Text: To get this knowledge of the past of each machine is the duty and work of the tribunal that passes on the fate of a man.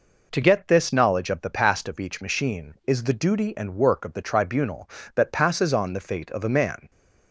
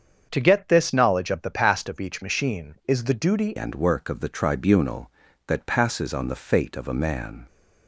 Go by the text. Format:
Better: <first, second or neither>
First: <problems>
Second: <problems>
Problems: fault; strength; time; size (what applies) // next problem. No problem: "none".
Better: first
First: none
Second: starts louder than the rest; until 1.3 s; 7 dB // changes voice at "and"; from 3.5 s on; 3.9 s long